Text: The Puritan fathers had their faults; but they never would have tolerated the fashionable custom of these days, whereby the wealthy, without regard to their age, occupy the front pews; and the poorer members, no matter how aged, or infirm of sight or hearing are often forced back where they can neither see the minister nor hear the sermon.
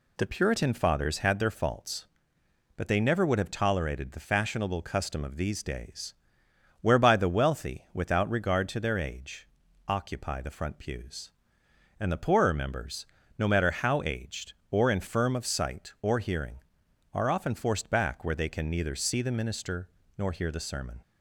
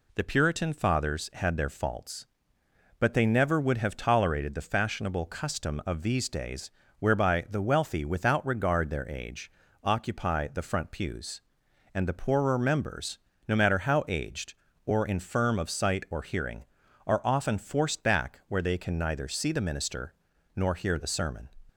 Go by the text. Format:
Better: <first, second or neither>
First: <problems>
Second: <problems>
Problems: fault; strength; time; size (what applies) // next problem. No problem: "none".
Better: first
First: pauses between "minister" and "nor"; slight; at 19.9 s; 0.26 s long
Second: skips "to"; at 8.9 s // pauses between "minister" and "nor"; at 20.1 s; 0.42 s long